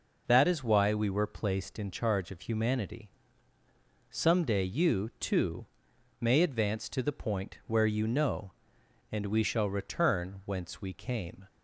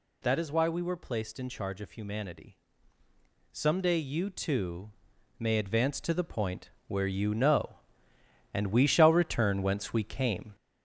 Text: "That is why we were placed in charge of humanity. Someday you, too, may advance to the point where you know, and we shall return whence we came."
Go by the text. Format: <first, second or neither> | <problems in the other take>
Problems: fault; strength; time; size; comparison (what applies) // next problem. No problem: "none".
first | gets louder; noticeable; throughout; 4.5 dB // pauses between "point" and "where"; slight; at 6.6 s; 0.18 s long